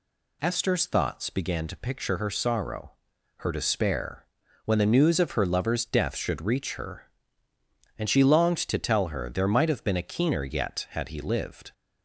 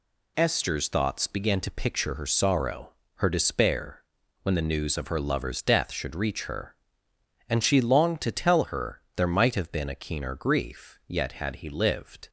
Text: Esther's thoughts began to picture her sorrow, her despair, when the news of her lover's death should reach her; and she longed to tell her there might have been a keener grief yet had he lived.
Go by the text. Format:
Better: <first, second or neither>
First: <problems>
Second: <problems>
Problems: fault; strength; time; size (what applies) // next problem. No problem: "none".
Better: second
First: skips "grief"; at 10.4 s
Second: none